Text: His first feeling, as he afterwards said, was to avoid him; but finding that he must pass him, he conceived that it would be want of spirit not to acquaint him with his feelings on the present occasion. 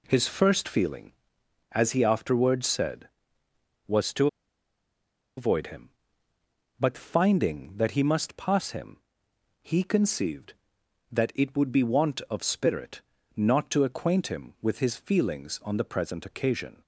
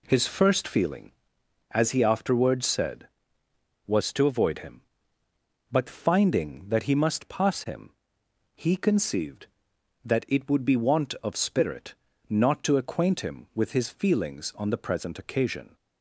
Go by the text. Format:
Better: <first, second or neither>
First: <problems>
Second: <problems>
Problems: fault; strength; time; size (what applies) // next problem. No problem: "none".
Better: second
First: pauses between "to" and "avoid"; at 4.2 s; 1.1 s long // pauses between "spirit" and "not"; slight; at 13.0 s; 0.34 s long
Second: pauses between "spirit" and "not"; slight; at 11.9 s; 0.34 s long